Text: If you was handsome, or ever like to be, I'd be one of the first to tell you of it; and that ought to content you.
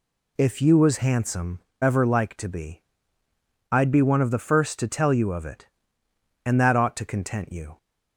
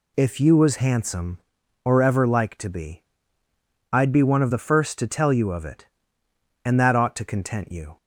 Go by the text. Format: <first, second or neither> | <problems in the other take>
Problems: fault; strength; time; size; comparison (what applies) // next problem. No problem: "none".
second | skips "or"; at 1.7 s